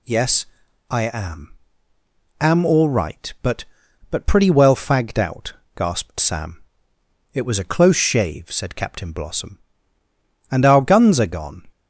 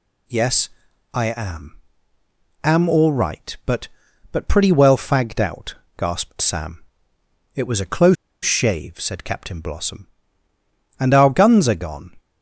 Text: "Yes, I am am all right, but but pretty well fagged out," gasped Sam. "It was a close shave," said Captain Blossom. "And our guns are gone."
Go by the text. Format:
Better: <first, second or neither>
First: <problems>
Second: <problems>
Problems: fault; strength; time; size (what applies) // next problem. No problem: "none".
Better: first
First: pauses between "am" and "am"; noticeable; at 1.5 s; 0.88 s long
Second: pauses between "am" and "am"; noticeable; at 1.7 s; 0.88 s long // pauses between "close" and "shave"; slight; at 8.1 s; 0.28 s long